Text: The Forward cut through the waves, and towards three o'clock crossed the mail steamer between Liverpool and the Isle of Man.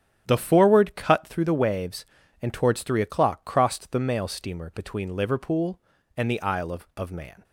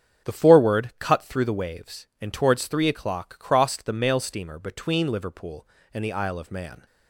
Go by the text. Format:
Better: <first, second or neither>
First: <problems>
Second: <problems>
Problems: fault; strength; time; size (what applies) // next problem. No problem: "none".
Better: second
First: starts louder than the rest; strong; until 1.2 s; 10 dB // says "of" twice; at 6.9 s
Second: starts louder than the rest; strong; until 1.3 s; 8 dB